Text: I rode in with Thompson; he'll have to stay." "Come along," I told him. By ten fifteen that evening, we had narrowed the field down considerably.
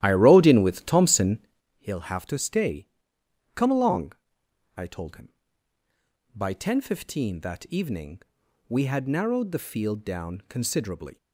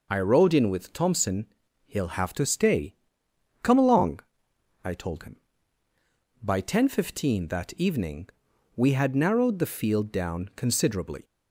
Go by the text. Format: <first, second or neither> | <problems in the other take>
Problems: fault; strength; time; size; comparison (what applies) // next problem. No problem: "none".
second | starts louder than the rest; strong; until 1.7 s; 13 dB